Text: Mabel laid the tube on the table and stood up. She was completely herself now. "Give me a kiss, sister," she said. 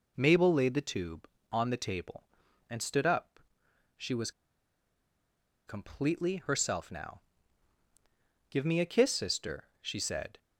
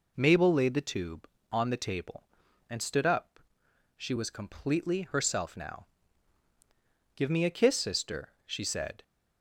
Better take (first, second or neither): second